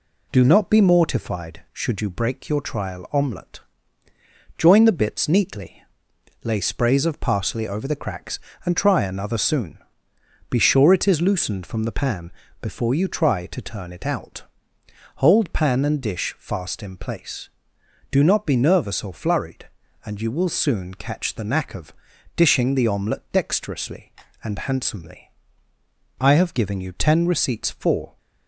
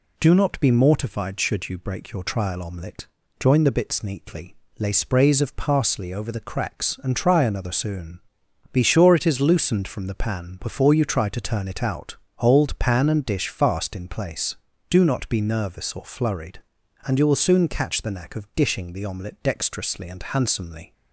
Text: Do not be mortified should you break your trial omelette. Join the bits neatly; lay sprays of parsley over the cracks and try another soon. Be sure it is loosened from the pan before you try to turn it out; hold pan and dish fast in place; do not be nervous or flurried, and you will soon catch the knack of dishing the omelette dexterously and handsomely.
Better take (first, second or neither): second